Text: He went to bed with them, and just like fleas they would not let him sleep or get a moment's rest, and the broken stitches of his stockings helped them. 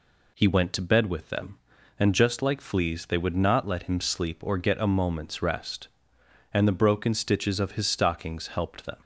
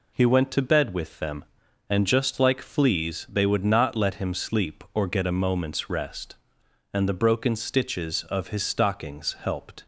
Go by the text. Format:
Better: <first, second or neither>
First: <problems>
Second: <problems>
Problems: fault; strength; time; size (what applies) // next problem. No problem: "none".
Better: first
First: none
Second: stops before "them"; at 9.8 s